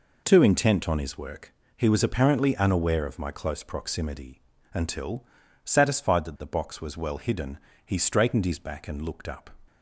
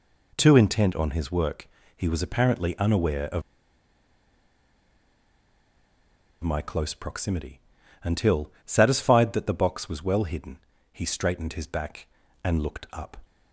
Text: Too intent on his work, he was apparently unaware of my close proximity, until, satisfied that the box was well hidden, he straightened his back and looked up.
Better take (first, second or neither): first